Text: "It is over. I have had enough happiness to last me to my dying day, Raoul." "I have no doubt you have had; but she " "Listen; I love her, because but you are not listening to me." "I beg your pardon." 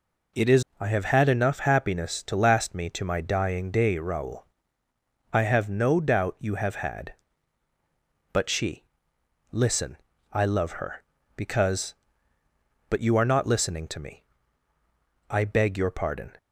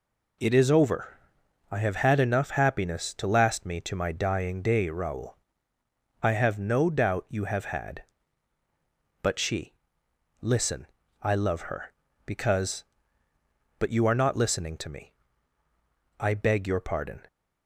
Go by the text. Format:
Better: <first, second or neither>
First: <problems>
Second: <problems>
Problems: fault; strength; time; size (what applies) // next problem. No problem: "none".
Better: second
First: skips "over"; at 0.7 s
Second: none